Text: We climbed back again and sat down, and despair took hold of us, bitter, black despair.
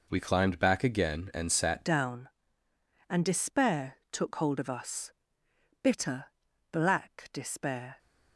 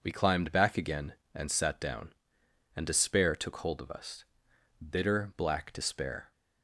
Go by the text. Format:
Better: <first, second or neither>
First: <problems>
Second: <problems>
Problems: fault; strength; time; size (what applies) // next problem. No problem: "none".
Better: second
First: changes voice at "down"; from 1.8 s on; 6.1 s long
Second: none